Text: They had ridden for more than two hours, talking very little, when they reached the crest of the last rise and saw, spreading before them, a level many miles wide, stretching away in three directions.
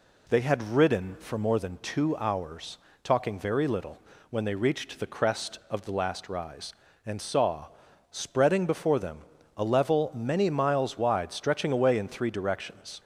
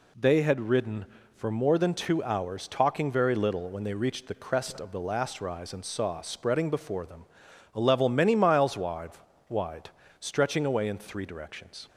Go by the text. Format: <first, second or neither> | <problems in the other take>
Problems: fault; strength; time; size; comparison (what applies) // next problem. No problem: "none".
first | says "wide" twice; at 9.4 s